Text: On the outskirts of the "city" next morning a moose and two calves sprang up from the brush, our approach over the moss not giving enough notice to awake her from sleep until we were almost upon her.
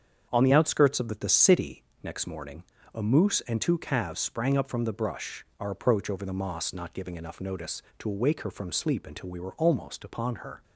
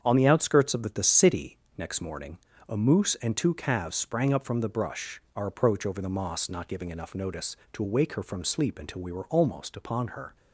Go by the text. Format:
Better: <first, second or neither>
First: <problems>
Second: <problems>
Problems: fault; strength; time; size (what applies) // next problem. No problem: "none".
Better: neither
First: starts louder than the rest; strong; until 1.3 s; 7 dB // pauses between "city" and "next"; slight; at 1.8 s; 0.18 s long // pauses between "morning" and "a"; slight; at 2.6 s; 0.28 s long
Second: starts louder than the rest; strong; until 1.0 s; 7.5 dB // pauses between "city" and "next"; slight; at 1.5 s; 0.18 s long // pauses between "morning" and "a"; slight; at 2.3 s; 0.28 s long